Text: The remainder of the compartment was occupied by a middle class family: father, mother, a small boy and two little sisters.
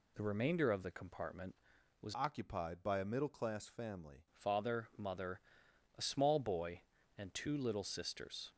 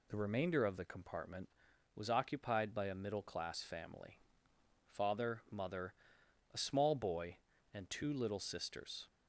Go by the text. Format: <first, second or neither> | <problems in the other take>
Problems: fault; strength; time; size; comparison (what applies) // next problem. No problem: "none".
second | changes voice from "occupied" to "family"; from 2.1 to 4.2 s; 2.1 s long